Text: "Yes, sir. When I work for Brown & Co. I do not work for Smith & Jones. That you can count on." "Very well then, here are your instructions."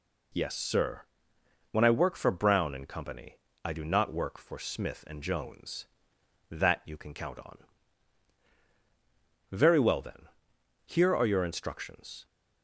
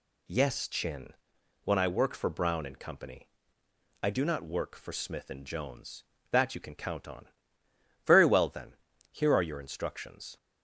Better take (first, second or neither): first